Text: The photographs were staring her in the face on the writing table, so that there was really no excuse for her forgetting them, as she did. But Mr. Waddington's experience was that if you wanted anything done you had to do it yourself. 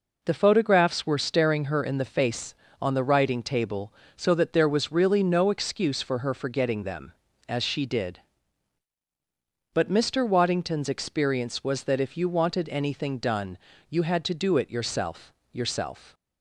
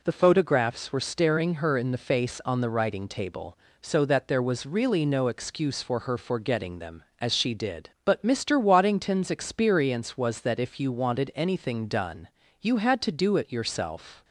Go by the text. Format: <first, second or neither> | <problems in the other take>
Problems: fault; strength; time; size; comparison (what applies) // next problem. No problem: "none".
second | pauses between "done" and "you"; slight; at 13.5 s; 0.32 s long; slight in the second // says "yourself" twice; at 15.5 s